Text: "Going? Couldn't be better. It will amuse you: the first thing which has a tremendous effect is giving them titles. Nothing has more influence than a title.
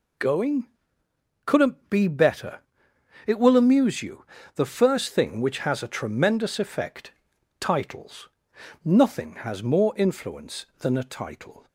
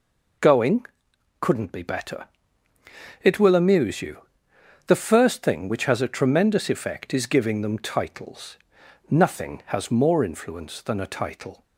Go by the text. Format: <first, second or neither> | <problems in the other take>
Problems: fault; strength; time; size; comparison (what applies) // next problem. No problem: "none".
second | skips "is giving them"; at 7.3 s